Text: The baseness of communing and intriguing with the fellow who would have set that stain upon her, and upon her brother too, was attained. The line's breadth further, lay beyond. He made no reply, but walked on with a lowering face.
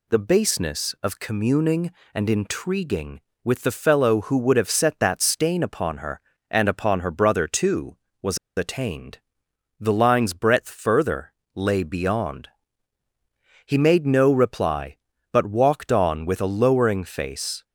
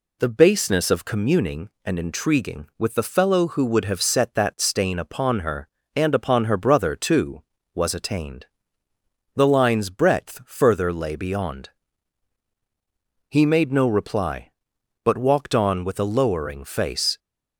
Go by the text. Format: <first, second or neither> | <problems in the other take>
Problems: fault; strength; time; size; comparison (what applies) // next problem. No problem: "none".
second | pauses between "was" and "attained"; slight; at 8.3 s; 0.19 s long